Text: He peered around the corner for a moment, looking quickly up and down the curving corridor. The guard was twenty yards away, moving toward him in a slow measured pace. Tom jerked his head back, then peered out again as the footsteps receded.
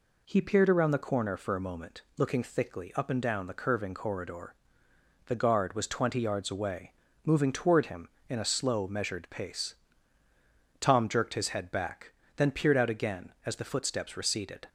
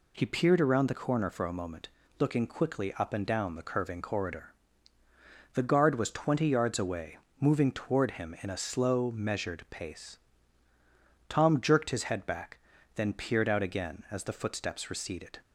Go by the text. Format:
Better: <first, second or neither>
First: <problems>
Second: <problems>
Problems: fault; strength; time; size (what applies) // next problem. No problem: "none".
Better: second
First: says "thickly" for "quickly"; at 2.4 s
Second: none